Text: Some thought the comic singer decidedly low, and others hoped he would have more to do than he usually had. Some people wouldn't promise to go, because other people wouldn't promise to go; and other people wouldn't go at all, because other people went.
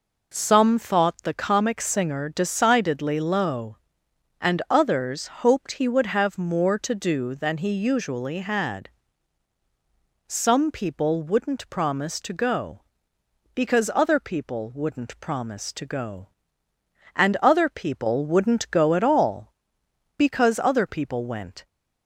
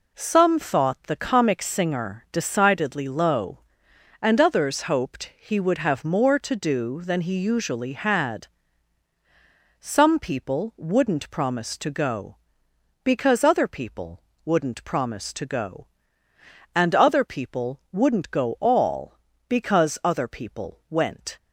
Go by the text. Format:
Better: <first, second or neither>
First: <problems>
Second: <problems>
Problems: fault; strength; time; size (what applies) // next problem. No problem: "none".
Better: first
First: none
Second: pauses between "people" and "wouldn't"; slight; at 14.2 s; 0.24 s long // skips "at"; at 18.5 s